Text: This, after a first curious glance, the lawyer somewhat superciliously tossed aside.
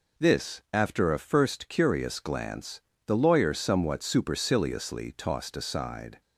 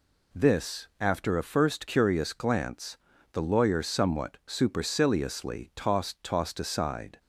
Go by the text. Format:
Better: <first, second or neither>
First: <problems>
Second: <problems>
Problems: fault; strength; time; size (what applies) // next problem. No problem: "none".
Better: first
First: none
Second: says "tossed" twice; at 6.2 s